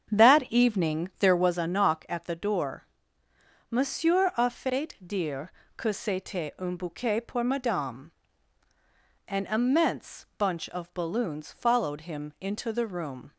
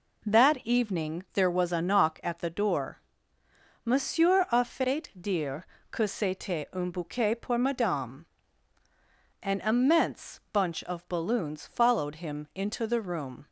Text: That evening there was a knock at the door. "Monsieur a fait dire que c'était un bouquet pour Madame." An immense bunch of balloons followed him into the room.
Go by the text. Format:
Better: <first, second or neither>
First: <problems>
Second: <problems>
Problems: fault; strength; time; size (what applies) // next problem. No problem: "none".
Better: second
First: starts louder than the rest; strong; until 1.6 s; 8 dB // pauses between "dire" and "que"; slight; at 5.5 s; 0.26 s long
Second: pauses between "dire" and "que"; slight; at 5.6 s; 0.26 s long